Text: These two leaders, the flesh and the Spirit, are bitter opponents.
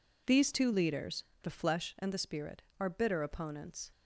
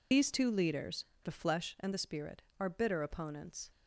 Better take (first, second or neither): first